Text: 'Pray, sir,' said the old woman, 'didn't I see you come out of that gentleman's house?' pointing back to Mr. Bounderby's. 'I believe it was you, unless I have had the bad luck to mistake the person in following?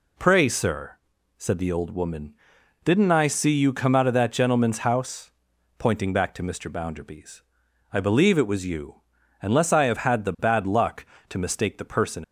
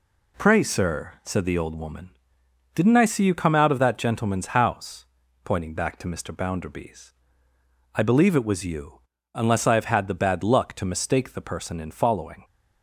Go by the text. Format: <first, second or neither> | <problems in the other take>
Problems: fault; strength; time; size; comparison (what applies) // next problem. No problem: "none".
second | stops before "in following"; at 12.2 s